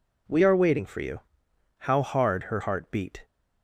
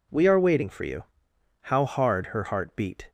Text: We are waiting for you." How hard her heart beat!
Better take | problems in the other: neither | none

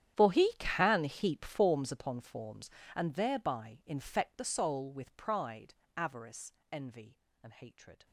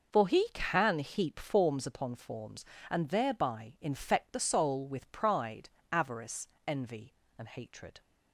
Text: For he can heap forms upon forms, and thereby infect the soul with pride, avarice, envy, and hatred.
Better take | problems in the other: second | gets quieter; strong; throughout; 23 dB

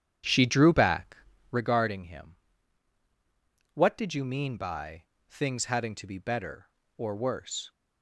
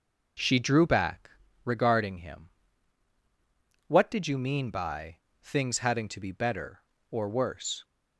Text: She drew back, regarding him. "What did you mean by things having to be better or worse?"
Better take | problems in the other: second | starts louder than the rest; strong; until 1.7 s; 9.5 dB // pauses between "by" and "things"; slight; at 5.0 s; 0.24 s long; slight in the second

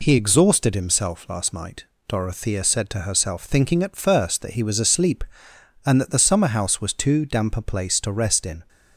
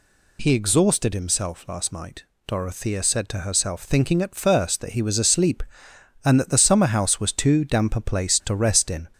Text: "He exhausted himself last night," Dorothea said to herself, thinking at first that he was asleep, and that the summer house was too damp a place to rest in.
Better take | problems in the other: first | gets louder; slight; throughout; 2 dB

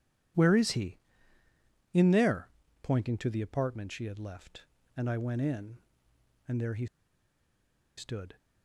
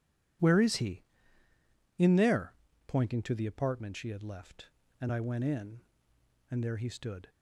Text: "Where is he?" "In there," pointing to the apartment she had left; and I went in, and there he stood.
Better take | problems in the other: second | pauses between "he" and "stood"; at 6.8 s; 1.1 s long

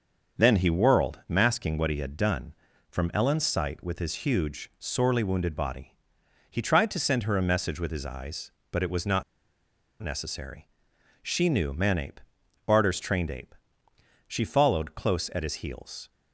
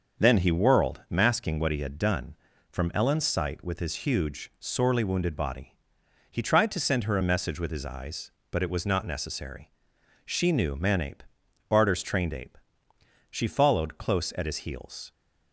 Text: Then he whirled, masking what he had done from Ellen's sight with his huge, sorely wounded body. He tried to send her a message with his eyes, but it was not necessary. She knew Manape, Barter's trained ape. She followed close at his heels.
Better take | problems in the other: second | starts louder than the rest; until 1.4 s; 6.5 dB; also in the second // pauses between "not" and "necessary"; noticeable; at 9.2 s; 0.79 s long

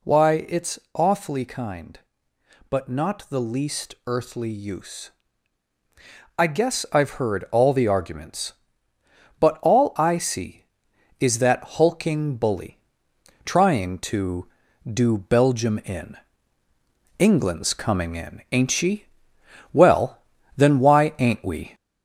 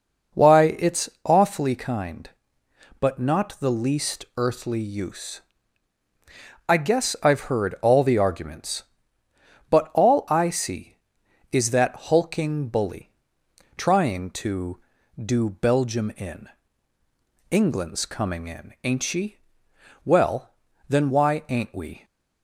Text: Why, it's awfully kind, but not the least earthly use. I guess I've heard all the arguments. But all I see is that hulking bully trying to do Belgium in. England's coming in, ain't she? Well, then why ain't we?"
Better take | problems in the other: second | gets louder; slight; throughout; 2.5 dB // pauses between "bully" and "trying"; noticeable; at 12.7 s; 0.66 s long; noticeable in the second

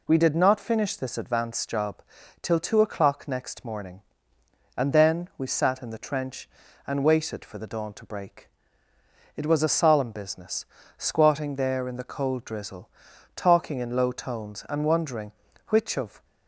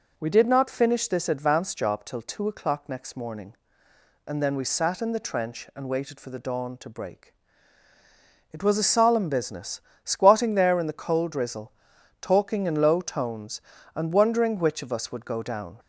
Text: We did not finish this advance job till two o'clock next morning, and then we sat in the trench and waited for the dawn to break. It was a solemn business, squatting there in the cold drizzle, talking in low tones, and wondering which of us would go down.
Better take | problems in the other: second | pauses between "job" and "till"; at 2.0 s; 0.40 s long // stops before "us would go down"; at 16.2 s

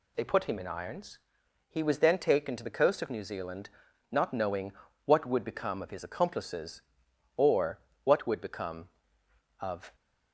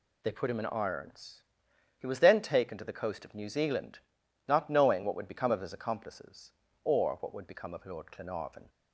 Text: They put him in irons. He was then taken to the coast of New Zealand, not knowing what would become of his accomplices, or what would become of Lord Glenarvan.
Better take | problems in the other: second | pauses between "knowing" and "what"; slight; at 4.7 s; 0.34 s long // pauses between "or" and "what"; slight; at 7.8 s; 0.24 s long // stops before "Lord Glenarvan"; at 9.9 s

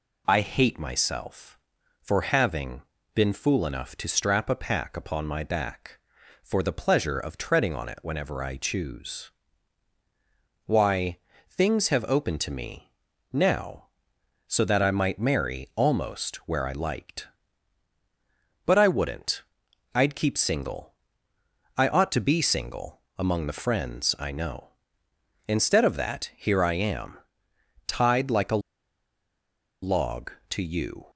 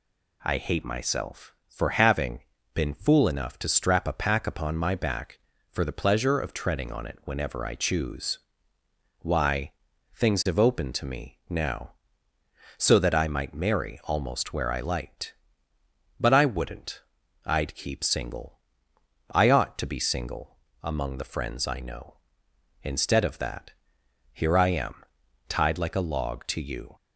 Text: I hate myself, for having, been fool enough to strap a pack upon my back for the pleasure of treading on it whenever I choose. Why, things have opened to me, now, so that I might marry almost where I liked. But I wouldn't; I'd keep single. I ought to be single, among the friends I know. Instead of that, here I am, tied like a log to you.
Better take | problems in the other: second | pauses between "a" and "log"; at 28.5 s; 1.2 s long

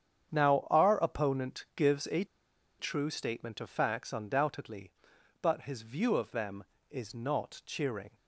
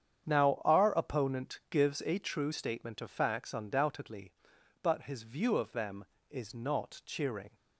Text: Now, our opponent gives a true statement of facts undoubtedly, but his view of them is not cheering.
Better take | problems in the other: second | starts louder than the rest; strong; until 1.3 s; 8.5 dB; strong in the second // pauses between "a" and "true"; noticeable; at 2.2 s; 0.54 s long

